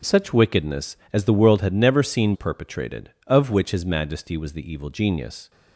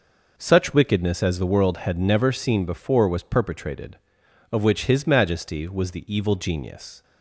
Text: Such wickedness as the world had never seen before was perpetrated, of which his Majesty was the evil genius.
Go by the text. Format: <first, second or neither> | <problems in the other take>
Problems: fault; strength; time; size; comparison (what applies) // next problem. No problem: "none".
second | skips "before was"; at 2.3 s